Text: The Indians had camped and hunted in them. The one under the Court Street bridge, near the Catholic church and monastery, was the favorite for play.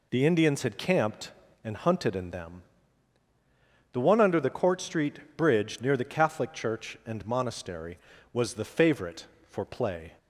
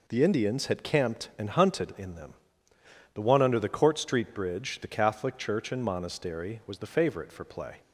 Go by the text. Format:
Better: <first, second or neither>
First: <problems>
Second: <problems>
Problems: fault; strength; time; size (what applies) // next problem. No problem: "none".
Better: first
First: none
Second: skips "near"; at 4.7 s